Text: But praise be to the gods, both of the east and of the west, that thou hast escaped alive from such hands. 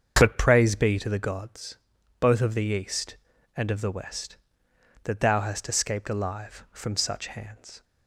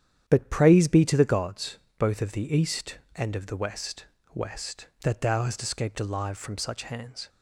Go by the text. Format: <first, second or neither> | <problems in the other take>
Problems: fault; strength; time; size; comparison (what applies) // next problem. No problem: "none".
first | starts louder than the rest; strong; until 1.2 s; 9.5 dB; strong in the first // says "west" twice; at 4.3 s